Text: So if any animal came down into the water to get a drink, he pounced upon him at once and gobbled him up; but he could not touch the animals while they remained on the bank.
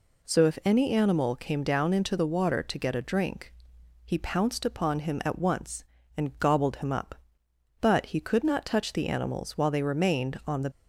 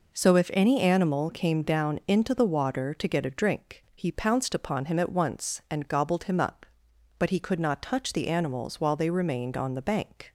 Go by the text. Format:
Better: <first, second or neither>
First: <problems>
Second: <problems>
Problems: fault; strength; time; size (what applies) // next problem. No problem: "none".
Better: second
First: stops before "bank"; at 10.7 s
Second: none